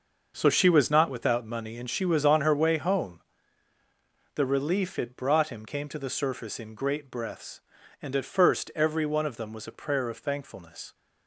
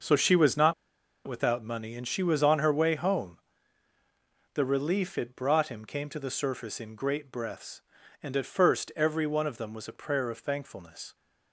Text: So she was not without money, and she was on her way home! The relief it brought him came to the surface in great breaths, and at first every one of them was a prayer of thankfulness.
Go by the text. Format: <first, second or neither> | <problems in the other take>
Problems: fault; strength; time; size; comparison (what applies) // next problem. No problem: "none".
first | starts louder than the rest; noticeable; until 1.5 s; 6 dB // pauses between "not" and "without"; noticeable; at 0.7 s; 0.53 s long